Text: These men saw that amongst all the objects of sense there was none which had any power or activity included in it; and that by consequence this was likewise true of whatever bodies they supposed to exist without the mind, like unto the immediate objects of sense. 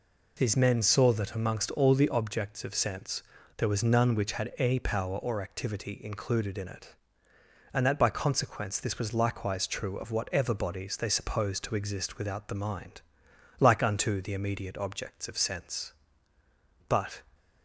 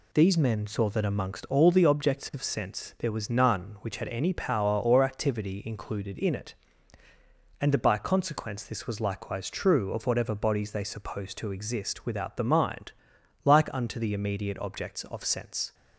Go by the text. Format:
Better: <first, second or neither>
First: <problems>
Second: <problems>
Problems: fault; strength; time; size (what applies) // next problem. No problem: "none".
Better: second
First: pauses between "sense" and "there"; slight; at 3.2 s; 0.34 s long // goes on to say "But"; slight; from 16.8 s on; 0.36 s long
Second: none